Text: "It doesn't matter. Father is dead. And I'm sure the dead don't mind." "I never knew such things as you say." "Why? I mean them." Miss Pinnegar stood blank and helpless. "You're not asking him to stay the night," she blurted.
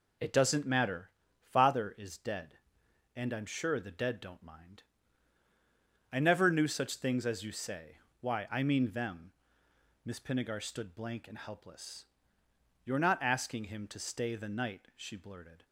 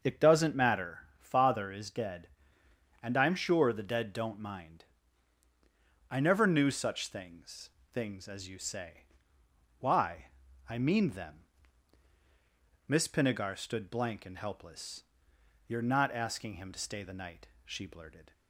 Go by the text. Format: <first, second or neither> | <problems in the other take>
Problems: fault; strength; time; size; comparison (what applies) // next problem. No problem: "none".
first | starts louder than the rest; until 1.2 s; 6.5 dB // says "things" twice; at 7.9 s